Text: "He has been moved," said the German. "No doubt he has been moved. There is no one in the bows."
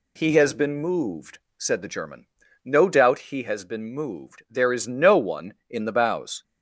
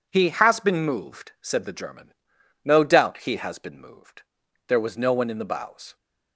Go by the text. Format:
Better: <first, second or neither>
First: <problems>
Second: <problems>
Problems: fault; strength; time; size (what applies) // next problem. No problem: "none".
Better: first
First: none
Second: says "was" for "is"; at 4.7 s